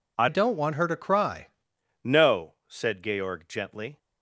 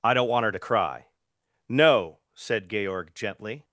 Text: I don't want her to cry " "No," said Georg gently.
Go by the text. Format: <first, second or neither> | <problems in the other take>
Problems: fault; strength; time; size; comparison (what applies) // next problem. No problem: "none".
second | changes voice from "don't" to "cry"; from 0.2 to 1.4 s; 1.2 s long